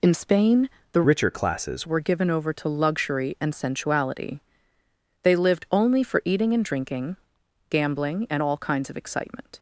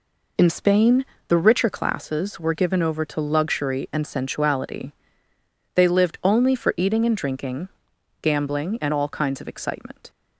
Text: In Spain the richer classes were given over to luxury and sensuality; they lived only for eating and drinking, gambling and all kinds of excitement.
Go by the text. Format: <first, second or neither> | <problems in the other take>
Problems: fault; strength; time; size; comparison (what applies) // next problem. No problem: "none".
second | pauses between "Spain" and "the"; slight; at 0.7 s; 0.22 s long; slight in the second // changes voice from "richer" to "classes"; from 1.0 to 1.8 s; 0.8 s long